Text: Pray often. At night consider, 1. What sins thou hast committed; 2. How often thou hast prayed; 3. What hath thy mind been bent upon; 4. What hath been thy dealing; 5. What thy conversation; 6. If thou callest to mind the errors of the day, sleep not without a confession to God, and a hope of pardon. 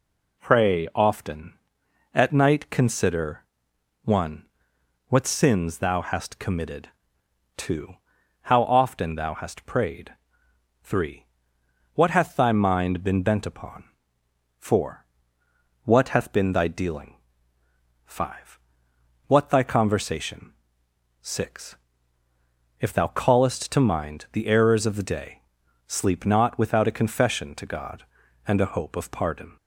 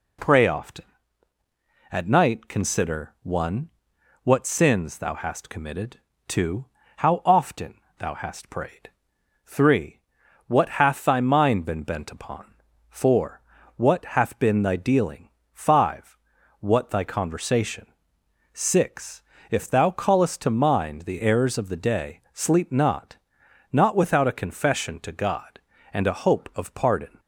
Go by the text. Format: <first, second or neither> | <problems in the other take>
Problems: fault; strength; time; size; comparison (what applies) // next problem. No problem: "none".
first | pauses between "often" and "thou"; slight; at 7.7 s; 0.24 s long // says "not" twice; at 23.7 s